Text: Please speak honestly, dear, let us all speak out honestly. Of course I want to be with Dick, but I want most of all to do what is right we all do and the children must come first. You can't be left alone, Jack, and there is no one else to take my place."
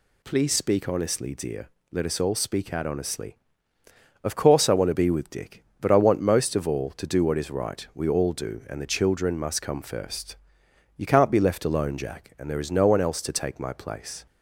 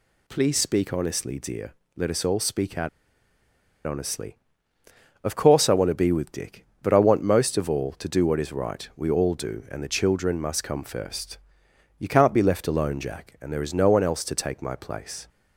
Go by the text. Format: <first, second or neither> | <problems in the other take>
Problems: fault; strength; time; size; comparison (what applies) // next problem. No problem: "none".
first | pauses between "out" and "honestly"; noticeable; at 2.8 s; 0.96 s long